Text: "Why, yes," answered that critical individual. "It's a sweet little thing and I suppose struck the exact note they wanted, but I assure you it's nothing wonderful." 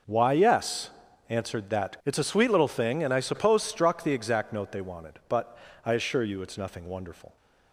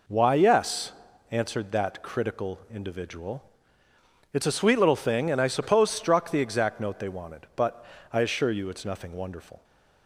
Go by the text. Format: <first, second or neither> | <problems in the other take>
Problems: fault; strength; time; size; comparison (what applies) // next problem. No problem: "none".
second | skips "critical individual"; at 2.0 s // pauses between "but" and "I"; slight; at 5.5 s; 0.26 s long; slight in the second